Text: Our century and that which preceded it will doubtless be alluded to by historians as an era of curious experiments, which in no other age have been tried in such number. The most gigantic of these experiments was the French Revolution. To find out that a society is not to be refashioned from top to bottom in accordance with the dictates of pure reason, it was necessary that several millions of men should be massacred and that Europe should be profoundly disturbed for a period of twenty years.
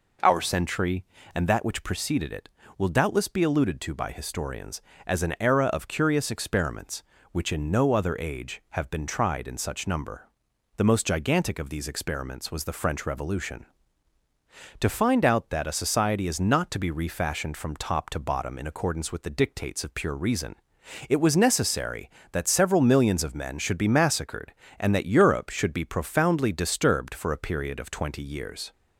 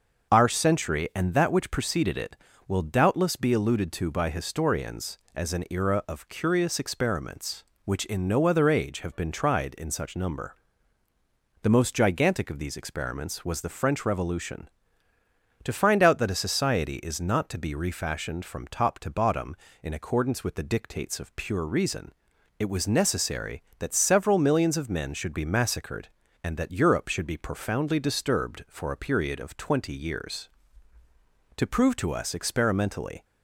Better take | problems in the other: first | starts louder than the rest; until 1.3 s; 6 dB // goes on to say "To prove to us experimentally"; strong; from 31.5 s on; 1.6 s long

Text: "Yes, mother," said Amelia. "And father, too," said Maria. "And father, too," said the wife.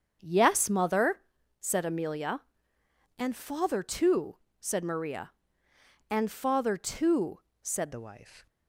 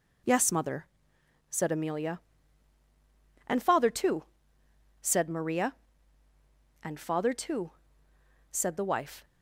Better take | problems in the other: second | starts louder than the rest; strong; until 1.2 s; 7 dB // changes voice at "the"; from 7.9 s on; 0.5 s long

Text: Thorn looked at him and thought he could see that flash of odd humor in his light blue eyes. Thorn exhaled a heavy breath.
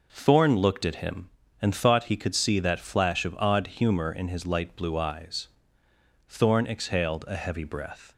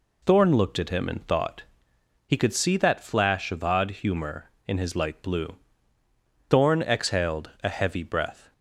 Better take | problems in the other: first | pauses between "thought" and "he"; noticeable; at 1.6 s; 0.64 s long // skips "eyes"; at 6.0 s

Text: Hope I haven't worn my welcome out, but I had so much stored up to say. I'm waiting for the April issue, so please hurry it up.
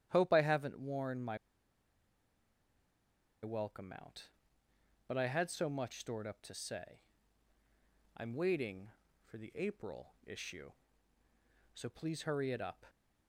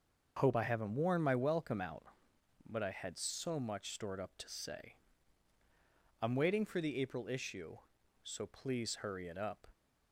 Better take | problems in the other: second | starts louder than the rest; strong; until 1.1 s; 10.5 dB; noticeable in the second // pauses between "my" and "welcome"; strong; at 1.3 s; 2.0 s long

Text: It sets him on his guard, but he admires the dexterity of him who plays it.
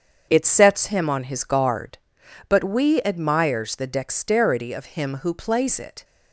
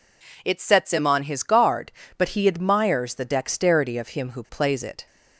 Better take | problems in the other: second | starts louder than the rest; until 1.3 s; 7 dB // says "we" for "he"; at 2.6 s

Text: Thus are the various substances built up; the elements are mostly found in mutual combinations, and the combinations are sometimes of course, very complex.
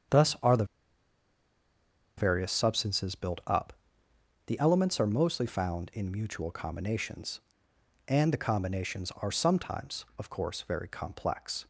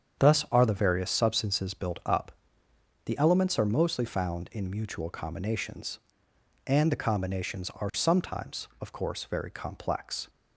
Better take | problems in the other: second | starts louder than the rest; strong; until 2.7 s; 8 dB; strong in the second // pauses between "the" and "various"; strong; at 0.6 s; 1.5 s long

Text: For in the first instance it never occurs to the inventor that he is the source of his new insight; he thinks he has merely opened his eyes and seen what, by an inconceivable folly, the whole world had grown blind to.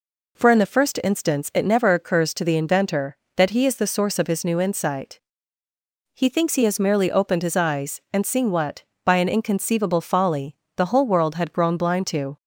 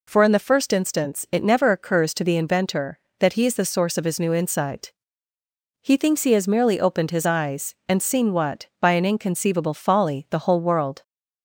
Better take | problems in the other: first | stops before "had grown blind to"; at 11.0 s

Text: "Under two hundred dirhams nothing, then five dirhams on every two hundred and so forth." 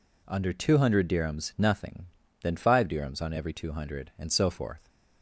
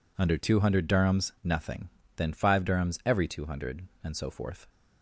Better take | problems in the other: first | skips "on"; at 3.0 s

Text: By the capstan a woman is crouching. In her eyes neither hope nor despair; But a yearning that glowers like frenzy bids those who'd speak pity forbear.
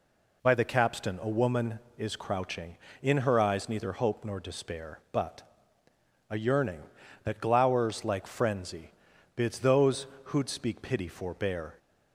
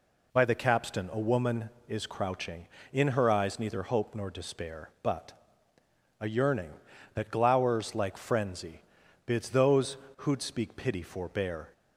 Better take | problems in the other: neither | pauses between "But" and "a"; noticeable; the same in both // pauses between "frenzy" and "bids"; the same in both // pauses between "those" and "who'd"; slight; the same in both

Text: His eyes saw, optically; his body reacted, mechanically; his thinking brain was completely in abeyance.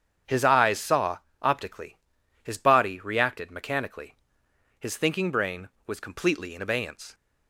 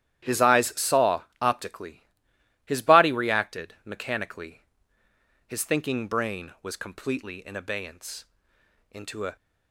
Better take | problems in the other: first | starts louder than the rest; strong; until 1.5 s; 12 dB; strong in the first // goes on to say "Into a"; slight; from 8.8 s on; 0.46 s long

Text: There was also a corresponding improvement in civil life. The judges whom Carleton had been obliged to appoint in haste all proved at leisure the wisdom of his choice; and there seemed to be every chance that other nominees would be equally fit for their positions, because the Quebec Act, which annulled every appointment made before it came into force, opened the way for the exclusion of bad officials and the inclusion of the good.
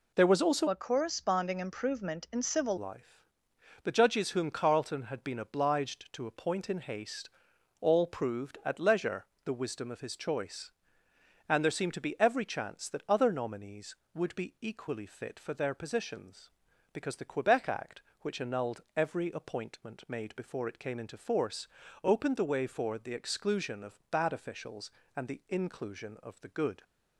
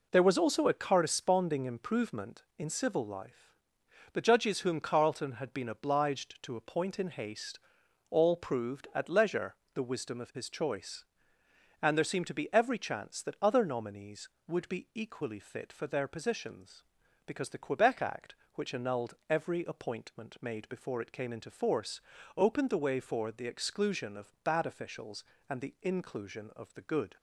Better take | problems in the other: second | changes voice from "a" to "civil"; from 0.6 to 2.7 s; 2.1 s long // pauses between "haste" and "all"; noticeable; at 7.2 s; 0.50 s long; noticeable in the second // pauses between "leisure" and "the"; slight; at 9.2 s; 0.20 s long; slight in the second // pauses between "annulled" and "every"; slight; at 18.8 s; 0.16 s long; slight in the second

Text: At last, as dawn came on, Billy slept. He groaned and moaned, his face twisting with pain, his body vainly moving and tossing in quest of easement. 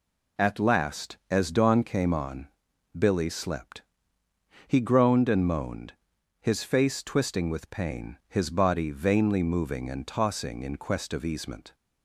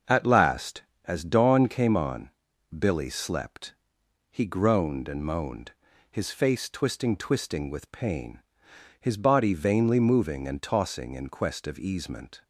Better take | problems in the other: first | says "twisting" twice; at 7.1 s

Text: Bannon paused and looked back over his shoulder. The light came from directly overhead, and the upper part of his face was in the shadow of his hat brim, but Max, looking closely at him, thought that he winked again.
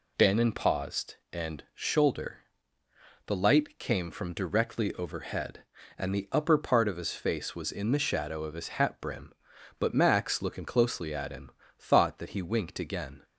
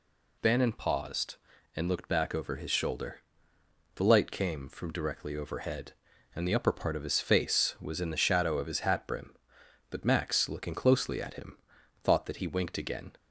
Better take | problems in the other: second | skips "looked back over his"; at 1.6 s

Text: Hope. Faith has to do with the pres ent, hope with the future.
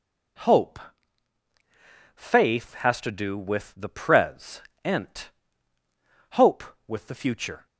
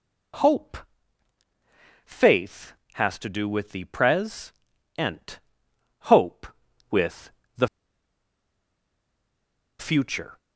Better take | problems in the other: first | pauses between "pres" and "ent"; noticeable; at 4.5 s; 0.48 s long; slight in the first // pauses between "with" and "the"; slight; at 7.3 s; 0.26 s long // pauses between "the" and "future"; strong; at 7.6 s; 2.1 s long

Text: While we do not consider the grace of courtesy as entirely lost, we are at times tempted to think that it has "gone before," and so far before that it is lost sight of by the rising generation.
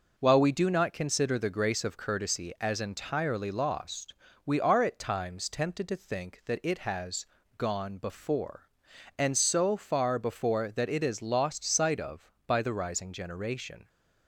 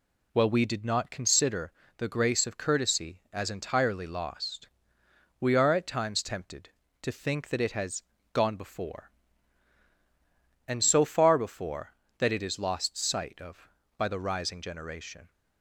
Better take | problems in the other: first | says "did" for "do"; at 0.6 s // pauses between "consider" and "the"; slight; at 1.7 s; 0.26 s long // pauses between "has" and "gone"; slight; at 8.0 s; 0.28 s long; slight in the first

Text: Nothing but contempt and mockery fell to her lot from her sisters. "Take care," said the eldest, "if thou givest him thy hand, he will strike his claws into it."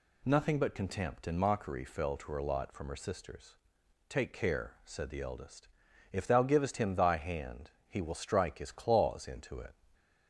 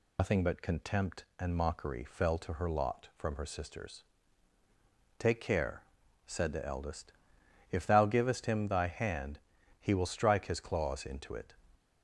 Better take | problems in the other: first | loses the start of "Nothing"; at 0.1 s; 110 ms

